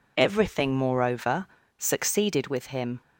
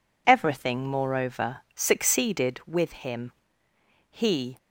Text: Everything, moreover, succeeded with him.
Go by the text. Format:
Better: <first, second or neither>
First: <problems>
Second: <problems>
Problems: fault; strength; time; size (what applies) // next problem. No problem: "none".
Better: first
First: none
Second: goes on to say "He"; slight; from 4.0 s on; 0.48 s long